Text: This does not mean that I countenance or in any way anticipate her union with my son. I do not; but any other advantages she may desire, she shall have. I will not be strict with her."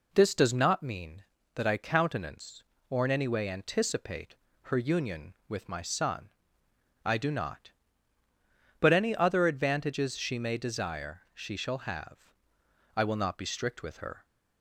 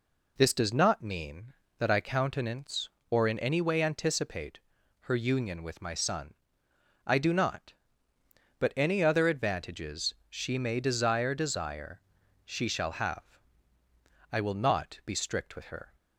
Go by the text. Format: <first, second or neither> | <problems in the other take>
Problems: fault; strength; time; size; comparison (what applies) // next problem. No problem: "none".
first | pauses between "anticipate" and "her"; at 4.5 s; 0.42 s long; slight in the first // pauses between "advantages" and "she"; slight; at 10.1 s; 0.16 s long // says "desire" twice; at 11.3 s